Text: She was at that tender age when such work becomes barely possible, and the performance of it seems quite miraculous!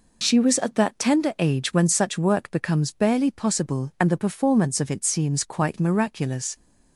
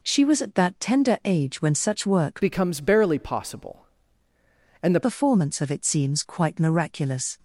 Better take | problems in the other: first | changes voice from "becomes" to "the"; from 2.4 to 4.9 s; 2.5 s long

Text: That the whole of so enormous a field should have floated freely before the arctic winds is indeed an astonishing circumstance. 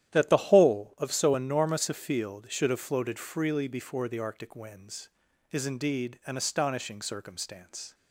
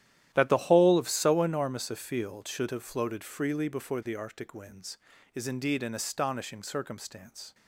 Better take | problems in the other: neither | starts louder than the rest; strong; the same in both

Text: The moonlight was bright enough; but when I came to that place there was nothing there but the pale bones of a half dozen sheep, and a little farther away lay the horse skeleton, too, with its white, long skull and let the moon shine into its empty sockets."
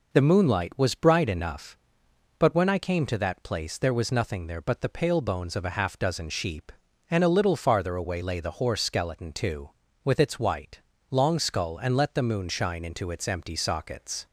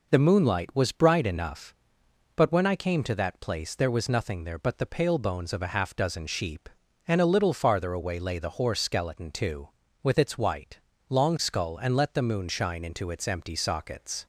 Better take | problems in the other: neither | none

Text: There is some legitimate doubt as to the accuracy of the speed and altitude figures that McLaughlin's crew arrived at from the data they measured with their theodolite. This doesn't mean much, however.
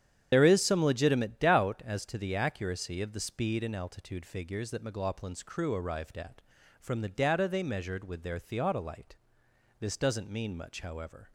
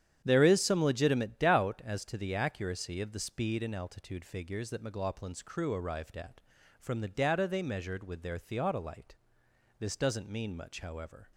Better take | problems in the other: second | loses the start of "There"; at 0.3 s; 75 ms // starts louder than the rest; strong; until 1.3 s; 9 dB; strong in the second

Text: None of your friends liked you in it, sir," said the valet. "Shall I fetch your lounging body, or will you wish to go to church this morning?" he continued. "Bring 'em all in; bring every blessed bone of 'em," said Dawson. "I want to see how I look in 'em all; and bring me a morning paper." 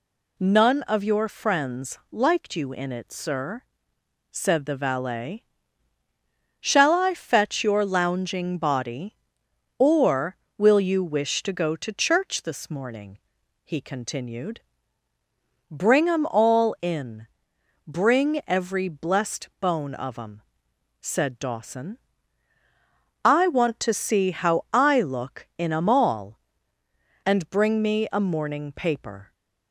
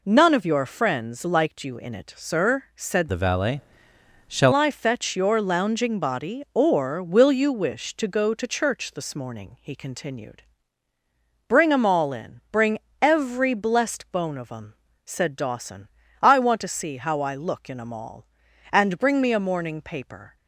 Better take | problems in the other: first | changes voice from "the" to "Shall"; from 3.1 to 4.5 s; 1.4 s long // pauses between "bring" and "every"; slight; at 12.7 s; 0.22 s long

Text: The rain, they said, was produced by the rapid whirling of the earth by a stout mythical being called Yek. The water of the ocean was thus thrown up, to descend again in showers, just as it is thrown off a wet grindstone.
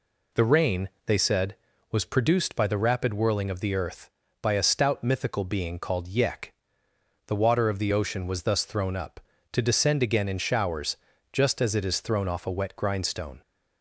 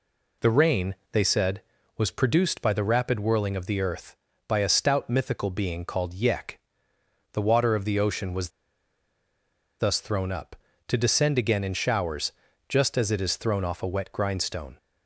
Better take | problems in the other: first | pauses between "was" and "thus"; strong; at 8.5 s; 1.2 s long

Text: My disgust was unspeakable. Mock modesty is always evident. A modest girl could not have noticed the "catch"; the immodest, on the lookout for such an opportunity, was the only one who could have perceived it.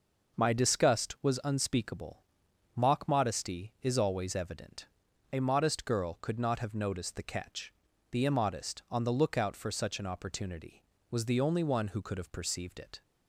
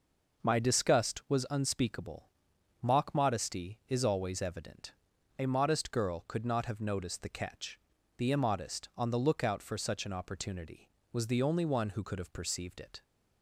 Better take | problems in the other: neither | none

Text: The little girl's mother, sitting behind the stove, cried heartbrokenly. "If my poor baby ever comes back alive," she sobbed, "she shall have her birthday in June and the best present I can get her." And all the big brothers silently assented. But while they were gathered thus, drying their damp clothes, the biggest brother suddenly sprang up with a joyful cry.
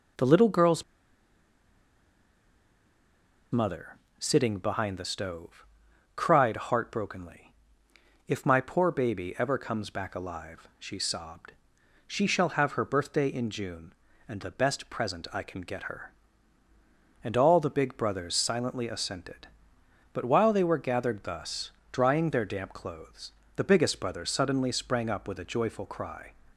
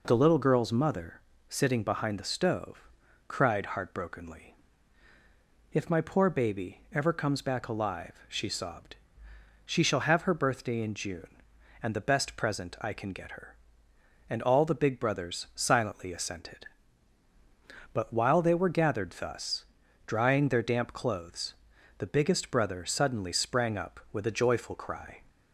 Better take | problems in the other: second | pauses between "girl's" and "mother"; strong; at 0.8 s; 2.7 s long

